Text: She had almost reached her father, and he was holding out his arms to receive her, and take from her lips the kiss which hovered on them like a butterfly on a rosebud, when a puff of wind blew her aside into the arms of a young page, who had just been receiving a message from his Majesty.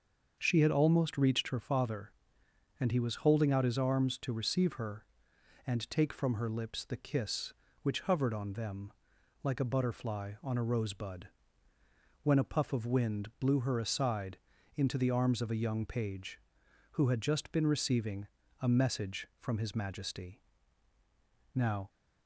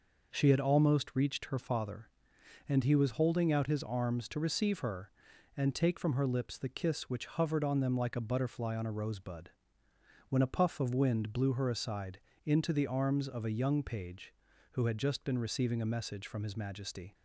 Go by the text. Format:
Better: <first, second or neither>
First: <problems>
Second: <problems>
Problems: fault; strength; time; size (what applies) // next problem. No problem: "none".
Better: second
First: starts louder than the rest; until 1.3 s; 6.5 dB // pauses between "them" and "like"; noticeable; at 8.9 s; 0.52 s long // pauses between "aside" and "into"; at 14.3 s; 0.38 s long // pauses between "receiving" and "a"; slight; at 18.2 s; 0.34 s long // goes on to say "Now"; slight; from 21.5 s on; 0.36 s long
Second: pauses between "aside" and "into"; slight; at 12.1 s; 0.28 s long